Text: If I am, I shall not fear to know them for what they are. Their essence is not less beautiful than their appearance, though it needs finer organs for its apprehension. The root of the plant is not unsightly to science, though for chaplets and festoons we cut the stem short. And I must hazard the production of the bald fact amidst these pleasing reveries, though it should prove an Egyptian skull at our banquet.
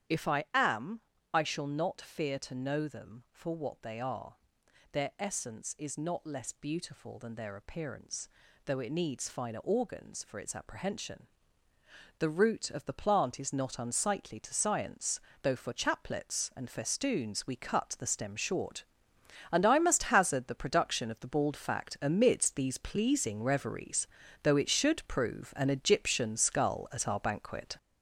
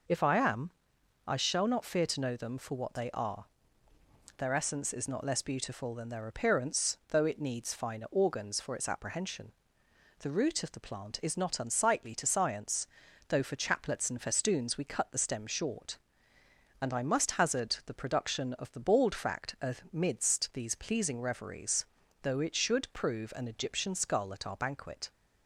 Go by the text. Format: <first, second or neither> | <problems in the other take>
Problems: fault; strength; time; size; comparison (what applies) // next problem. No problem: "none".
second | gets louder; noticeable; throughout; 5.5 dB // starts louder than the rest; strong; until 1.5 s; 9.5 dB